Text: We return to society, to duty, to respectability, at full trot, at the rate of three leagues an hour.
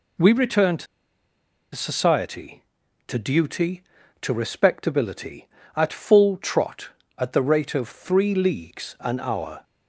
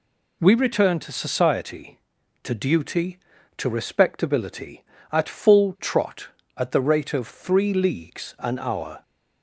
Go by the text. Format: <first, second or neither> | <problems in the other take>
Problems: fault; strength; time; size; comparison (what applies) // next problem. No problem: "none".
second | pauses between "to" and "society"; noticeable; at 0.8 s; 0.88 s long